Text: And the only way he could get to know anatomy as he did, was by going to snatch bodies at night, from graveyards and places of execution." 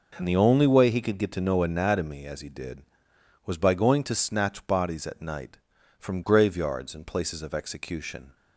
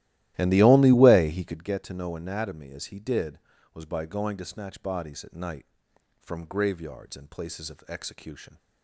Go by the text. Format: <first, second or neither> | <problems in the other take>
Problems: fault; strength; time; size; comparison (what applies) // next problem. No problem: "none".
first | starts louder than the rest; strong; until 1.6 s; 15 dB